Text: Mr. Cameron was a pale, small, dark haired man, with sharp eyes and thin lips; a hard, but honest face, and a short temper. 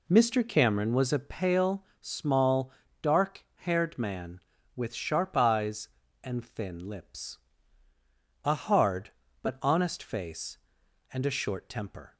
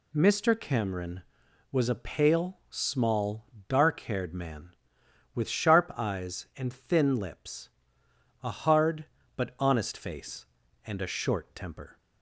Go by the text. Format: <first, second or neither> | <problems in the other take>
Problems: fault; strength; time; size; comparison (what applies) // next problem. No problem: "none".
second | starts louder than the rest; slight; until 1.5 s; 2.5 dB